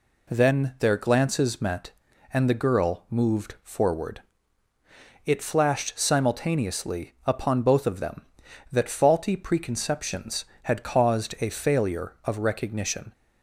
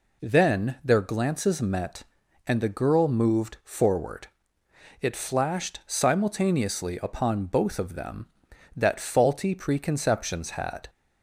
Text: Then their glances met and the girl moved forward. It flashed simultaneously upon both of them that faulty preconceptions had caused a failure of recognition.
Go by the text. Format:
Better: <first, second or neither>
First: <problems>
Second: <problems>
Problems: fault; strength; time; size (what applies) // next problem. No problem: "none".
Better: first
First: none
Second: stops before "caused a failure of recognition"; at 10.8 s